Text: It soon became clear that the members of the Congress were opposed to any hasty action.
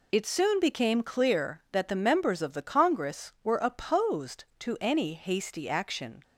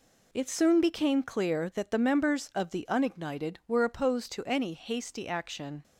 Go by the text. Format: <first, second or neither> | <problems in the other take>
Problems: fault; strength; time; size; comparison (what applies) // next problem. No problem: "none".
first | says "Unignited" for "Congress"; at 2.8 s